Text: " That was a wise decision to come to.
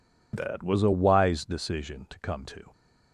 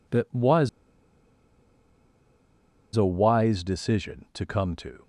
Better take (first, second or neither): first